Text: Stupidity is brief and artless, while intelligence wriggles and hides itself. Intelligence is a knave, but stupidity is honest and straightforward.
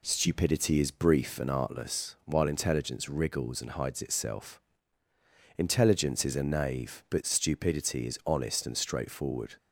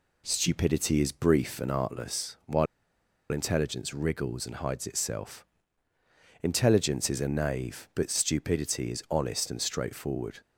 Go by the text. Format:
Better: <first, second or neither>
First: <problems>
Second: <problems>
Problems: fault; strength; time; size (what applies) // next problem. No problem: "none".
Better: first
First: none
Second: pauses between "while" and "intelligence"; noticeable; at 2.6 s; 0.64 s long